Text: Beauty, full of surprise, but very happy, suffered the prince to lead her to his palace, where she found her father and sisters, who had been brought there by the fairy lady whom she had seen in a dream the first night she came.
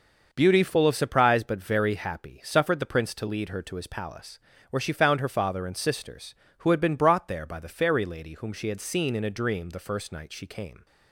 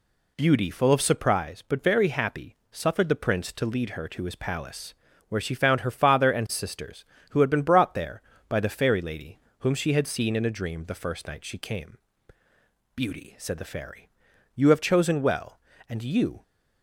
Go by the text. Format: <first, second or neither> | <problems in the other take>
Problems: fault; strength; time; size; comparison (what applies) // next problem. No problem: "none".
first | pauses between "lady" and "whom"; slight; at 9.3 s; 0.22 s long // goes on to say "Beauty said the fairy you have chosen well and you"; strong; from 12.9 s on; 3.4 s long